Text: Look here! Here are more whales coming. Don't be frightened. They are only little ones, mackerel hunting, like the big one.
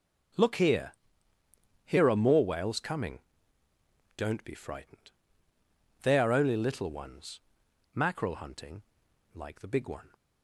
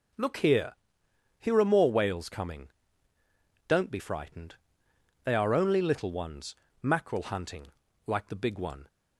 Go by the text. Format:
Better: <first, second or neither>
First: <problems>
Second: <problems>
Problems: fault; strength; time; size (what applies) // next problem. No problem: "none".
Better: neither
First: none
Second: none